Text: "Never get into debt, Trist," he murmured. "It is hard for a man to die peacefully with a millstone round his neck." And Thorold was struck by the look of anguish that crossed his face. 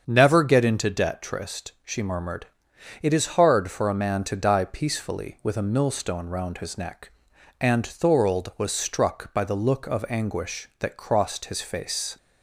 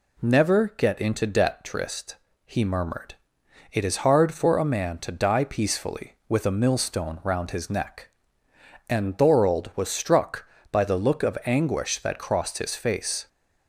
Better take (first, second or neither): second